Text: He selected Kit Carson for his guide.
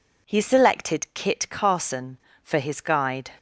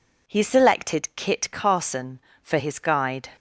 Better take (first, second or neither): neither